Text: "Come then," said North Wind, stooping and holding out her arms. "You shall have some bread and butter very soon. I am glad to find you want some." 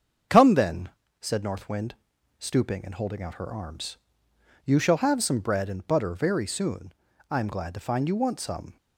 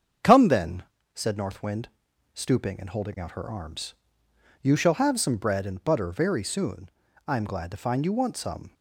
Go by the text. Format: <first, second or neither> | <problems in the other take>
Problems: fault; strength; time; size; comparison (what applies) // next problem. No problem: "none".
neither | starts louder than the rest; the same in both